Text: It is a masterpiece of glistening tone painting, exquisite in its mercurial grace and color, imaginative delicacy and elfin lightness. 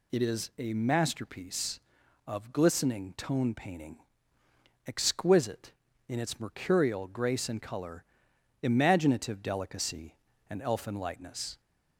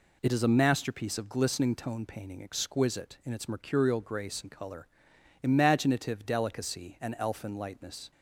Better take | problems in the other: neither | none

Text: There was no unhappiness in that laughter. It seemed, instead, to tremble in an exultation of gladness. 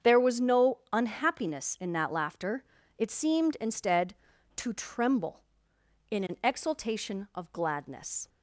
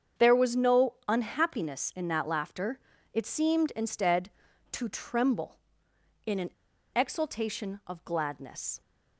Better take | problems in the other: first | starts louder than the rest; strong; until 1.3 s; 7.5 dB; strong in the first // pauses between "an" and "exultation"; at 6.4 s; 0.44 s long

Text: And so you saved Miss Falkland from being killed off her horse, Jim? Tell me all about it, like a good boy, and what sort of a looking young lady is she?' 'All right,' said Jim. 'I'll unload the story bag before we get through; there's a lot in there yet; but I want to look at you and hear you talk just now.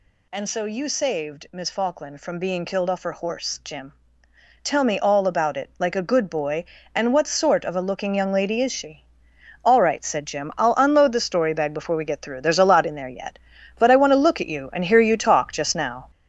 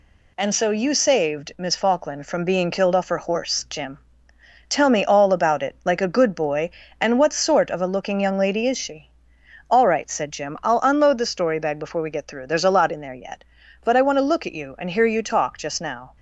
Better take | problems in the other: second | gets louder; noticeable; throughout; 6 dB

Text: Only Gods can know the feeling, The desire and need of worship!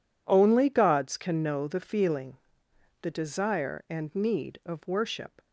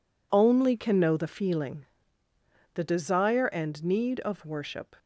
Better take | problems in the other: first | skips "Gods"; at 0.7 s

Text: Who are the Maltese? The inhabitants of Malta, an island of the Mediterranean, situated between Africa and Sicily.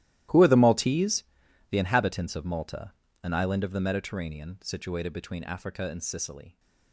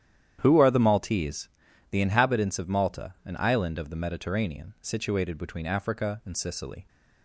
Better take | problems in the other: second | gets quieter; strong; throughout; 18.5 dB // starts louder than the rest; strong; until 1.7 s; 14.5 dB; strong in the second

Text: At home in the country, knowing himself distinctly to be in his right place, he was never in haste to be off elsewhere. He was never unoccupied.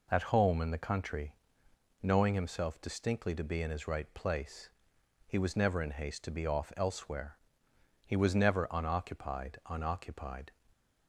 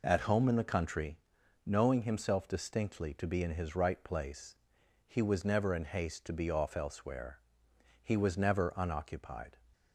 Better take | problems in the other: second | says "unoccupied" twice; at 9.6 s

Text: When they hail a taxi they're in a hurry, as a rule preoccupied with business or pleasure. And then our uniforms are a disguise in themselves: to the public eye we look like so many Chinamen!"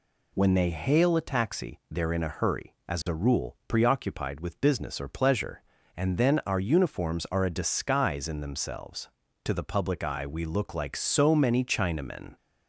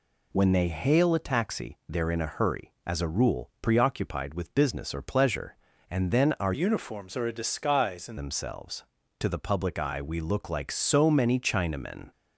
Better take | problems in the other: first | changes voice from "uniforms" to "in"; from 6.5 to 8.1 s; 1.6 s long

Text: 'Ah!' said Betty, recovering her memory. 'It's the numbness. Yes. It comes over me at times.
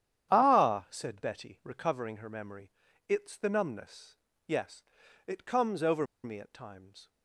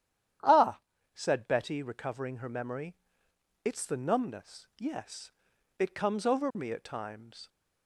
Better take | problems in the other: second | starts louder than the rest; strong; until 1.3 s; 10 dB; strong in the second // pauses between "over" and "me"; slight; at 6.0 s; 0.19 s long

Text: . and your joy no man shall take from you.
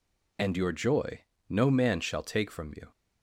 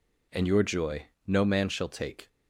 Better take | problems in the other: first | pauses between "joy" and "no"; slight; at 1.0 s; 0.20 s long; slight in the first // stops before "from you"; at 2.2 s

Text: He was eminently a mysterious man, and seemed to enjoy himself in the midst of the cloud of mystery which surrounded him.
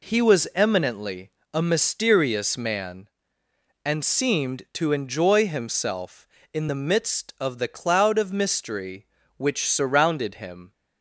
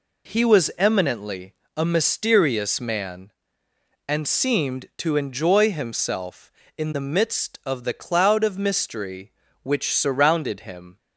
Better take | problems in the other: neither | pauses between "eminently" and "a"; slight; the same in both

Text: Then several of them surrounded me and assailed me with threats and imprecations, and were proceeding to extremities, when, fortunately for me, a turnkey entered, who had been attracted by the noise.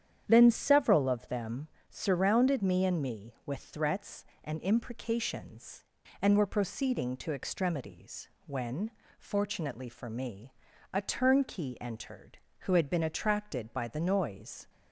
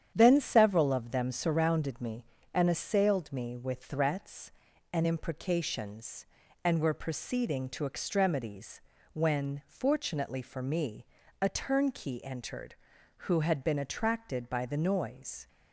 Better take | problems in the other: second | starts louder than the rest; strong; until 1.2 s; 9 dB; strong in the second // pauses between "them" and "surrounded"; slight; at 1.6 s; 0.20 s long // skips "assailed"; at 3.0 s

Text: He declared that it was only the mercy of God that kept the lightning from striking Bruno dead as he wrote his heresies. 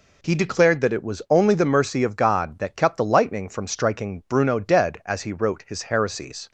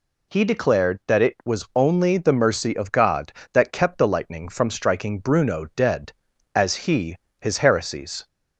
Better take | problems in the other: first | skips "wrote"; at 7.2 s

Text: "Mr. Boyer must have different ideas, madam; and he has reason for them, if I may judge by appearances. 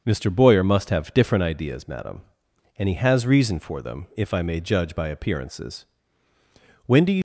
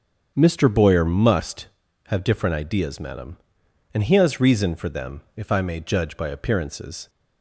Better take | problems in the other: second | starts louder than the rest; until 1.0 s; 6.5 dB; strong in the second // goes on to say "When do you"; slight; from 6.8 s on; 0.36 s long

